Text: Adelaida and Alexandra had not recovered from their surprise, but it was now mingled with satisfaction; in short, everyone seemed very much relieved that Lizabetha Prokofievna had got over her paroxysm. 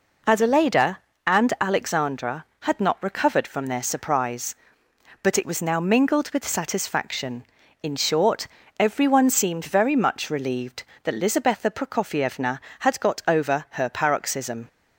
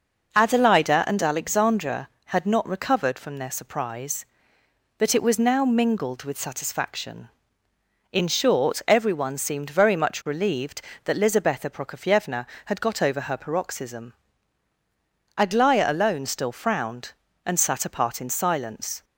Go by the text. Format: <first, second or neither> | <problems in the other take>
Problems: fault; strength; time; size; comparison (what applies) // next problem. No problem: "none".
first | goes on to say "Aglaya alone still frowned and sat apart in silence"; strong; from 15.3 s on; 3.6 s long